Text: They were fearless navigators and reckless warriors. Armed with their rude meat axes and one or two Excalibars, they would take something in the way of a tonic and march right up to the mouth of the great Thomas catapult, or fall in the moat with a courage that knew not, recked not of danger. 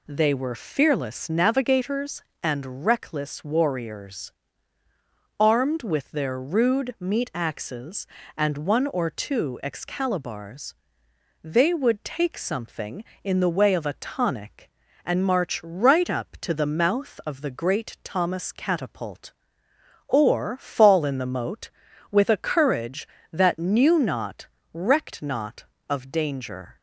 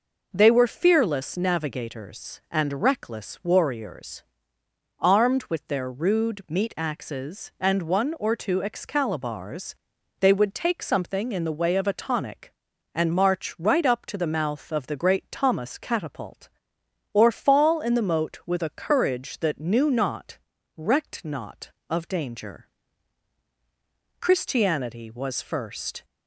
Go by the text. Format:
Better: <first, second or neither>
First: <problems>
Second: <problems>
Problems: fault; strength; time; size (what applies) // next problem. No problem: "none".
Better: first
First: none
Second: goes on to say "Christianity was first"; strong; from 24.2 s on; 1.8 s long